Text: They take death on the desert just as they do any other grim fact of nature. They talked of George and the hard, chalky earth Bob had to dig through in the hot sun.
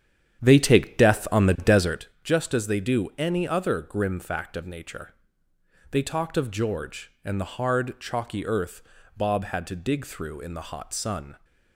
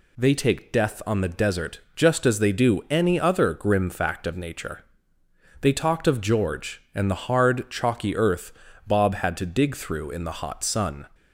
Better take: second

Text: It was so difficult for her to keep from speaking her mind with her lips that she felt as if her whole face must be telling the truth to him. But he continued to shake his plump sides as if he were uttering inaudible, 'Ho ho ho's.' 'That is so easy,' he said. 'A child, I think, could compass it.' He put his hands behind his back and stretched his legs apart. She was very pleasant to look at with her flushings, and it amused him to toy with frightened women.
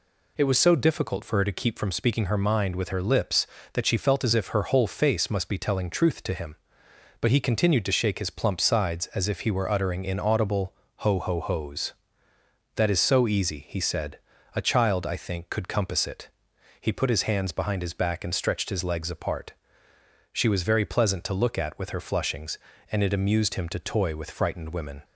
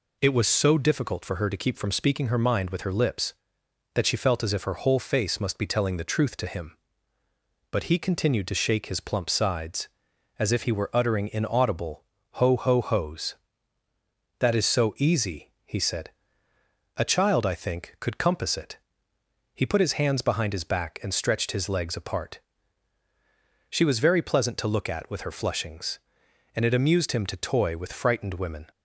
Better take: second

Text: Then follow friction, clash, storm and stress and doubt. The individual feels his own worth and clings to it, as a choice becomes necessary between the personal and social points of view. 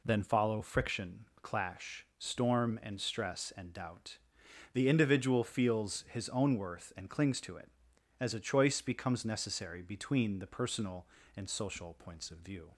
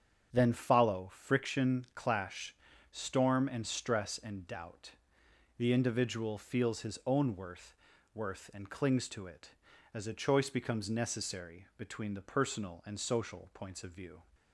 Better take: first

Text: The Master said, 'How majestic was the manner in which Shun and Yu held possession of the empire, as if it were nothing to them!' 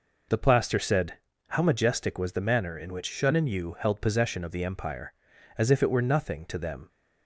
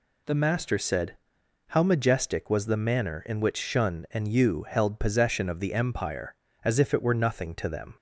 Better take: second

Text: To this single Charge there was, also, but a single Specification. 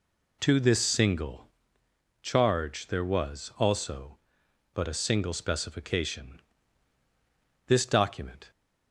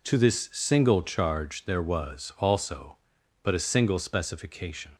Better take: second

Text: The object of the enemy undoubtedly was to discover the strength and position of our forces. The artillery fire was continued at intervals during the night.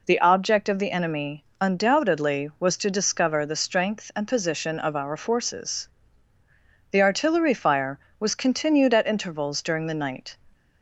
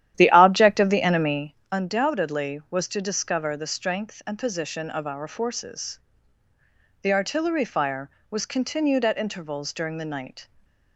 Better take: first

